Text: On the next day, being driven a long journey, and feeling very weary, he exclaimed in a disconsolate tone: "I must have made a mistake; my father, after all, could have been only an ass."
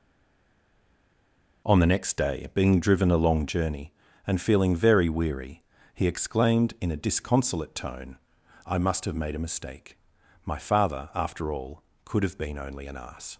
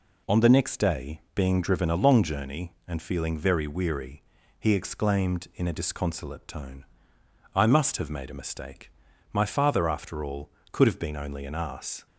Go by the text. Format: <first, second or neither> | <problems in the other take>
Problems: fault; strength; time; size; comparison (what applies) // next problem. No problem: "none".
second | stays silent before the first word; noticeable; until 1.6 s; 1.6 s long